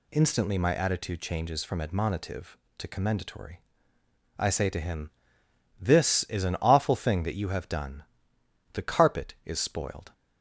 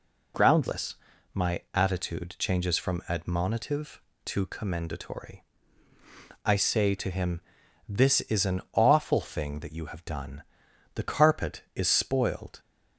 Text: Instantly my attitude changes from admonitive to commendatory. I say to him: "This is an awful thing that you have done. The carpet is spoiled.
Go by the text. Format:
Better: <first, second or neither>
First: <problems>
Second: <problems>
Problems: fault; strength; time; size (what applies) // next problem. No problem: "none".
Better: first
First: none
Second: says "Groundless" for "Instantly"; at 0.3 s